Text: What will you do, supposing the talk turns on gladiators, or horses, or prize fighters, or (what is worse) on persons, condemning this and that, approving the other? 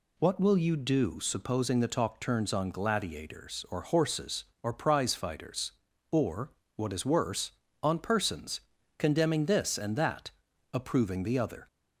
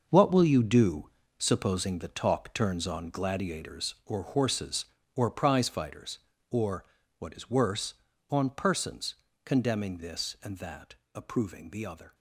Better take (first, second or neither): first